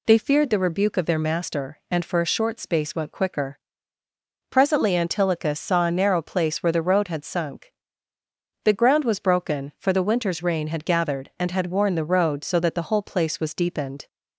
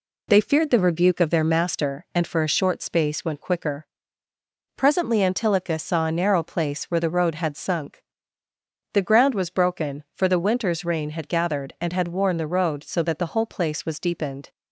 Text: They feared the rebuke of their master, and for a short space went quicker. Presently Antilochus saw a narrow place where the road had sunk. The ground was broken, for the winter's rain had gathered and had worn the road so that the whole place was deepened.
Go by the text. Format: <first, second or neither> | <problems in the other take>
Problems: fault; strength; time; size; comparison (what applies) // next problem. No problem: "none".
neither | none